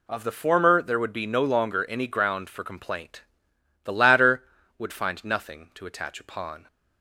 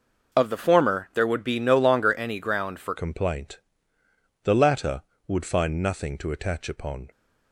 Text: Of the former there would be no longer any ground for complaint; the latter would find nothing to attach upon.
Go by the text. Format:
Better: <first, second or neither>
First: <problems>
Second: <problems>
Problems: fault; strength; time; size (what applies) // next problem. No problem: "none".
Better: first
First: none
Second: changes voice at "complaint"; from 2.9 s on; 4.2 s long